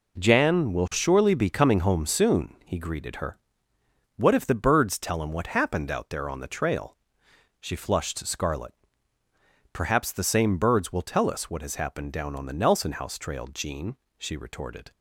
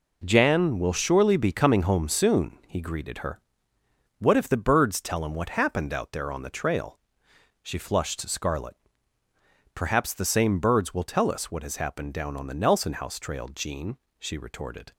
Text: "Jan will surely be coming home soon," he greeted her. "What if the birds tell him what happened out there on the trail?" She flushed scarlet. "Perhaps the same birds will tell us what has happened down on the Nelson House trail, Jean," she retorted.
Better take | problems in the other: neither | none

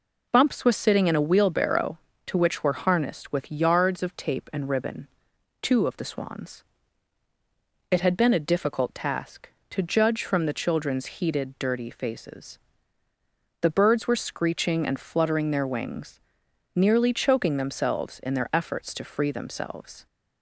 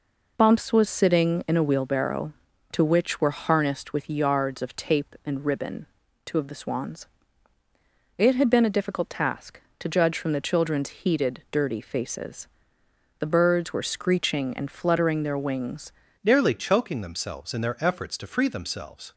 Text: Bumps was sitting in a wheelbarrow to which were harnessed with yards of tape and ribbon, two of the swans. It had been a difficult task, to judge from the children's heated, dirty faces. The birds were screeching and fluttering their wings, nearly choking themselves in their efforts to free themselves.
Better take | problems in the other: first | changes voice at "nearly"; from 16.2 s on; 2.9 s long

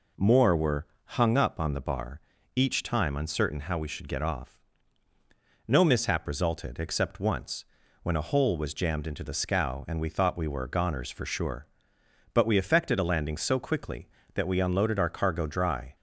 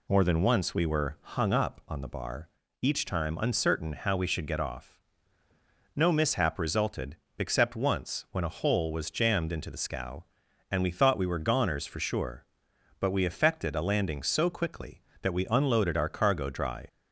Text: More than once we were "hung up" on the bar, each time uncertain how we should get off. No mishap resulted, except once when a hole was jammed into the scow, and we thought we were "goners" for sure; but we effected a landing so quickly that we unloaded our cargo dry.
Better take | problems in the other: second | skips "than once we"; at 0.5 s // pauses between "were" and "hung"; slight; at 0.8 s; 0.20 s long // pauses between "once" and "when"; at 7.6 s; 0.38 s long

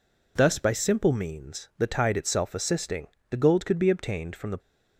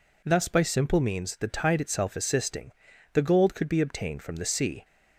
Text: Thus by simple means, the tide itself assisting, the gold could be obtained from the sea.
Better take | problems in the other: second | stops before "sea"; at 4.5 s

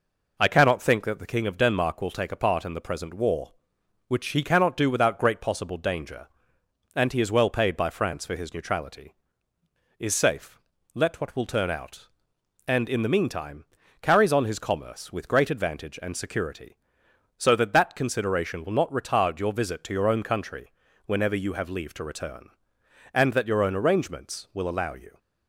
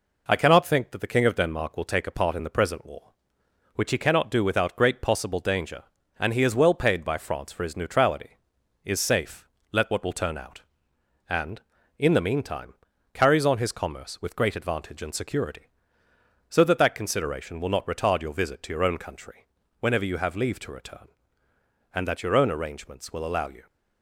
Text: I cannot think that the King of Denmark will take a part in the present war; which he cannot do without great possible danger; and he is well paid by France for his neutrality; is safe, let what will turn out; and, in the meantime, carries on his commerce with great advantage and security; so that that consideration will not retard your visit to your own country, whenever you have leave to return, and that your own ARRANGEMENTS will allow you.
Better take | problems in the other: neither | none

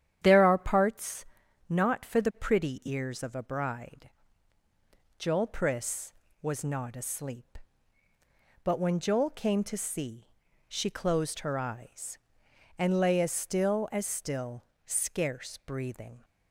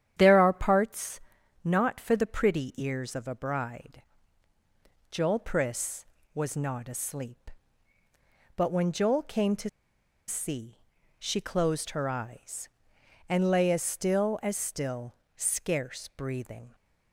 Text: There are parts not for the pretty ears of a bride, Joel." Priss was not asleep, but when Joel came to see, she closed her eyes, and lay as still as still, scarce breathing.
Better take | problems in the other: first | starts louder than the rest; strong; until 1.1 s; 10 dB; strong in the first // pauses between "parts" and "not"; at 1.2 s; 0.42 s long; also in the first // pauses between "to" and "see"; noticeable; at 9.6 s; 0.59 s long

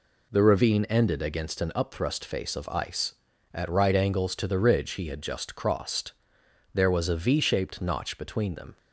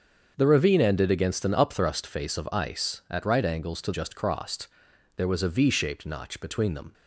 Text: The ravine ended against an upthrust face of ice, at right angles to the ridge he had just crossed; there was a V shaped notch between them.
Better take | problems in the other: first | starts louder than the rest; until 1.3 s; 6.5 dB // skips "the ridge he had"; at 3.9 s

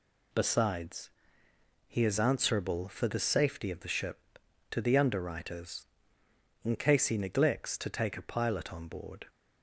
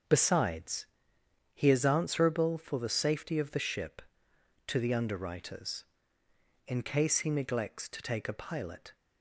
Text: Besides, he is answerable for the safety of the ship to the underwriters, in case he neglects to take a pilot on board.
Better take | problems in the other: first | starts louder than the rest; until 1.7 s; 6.5 dB // stops before "on board"; at 8.9 s

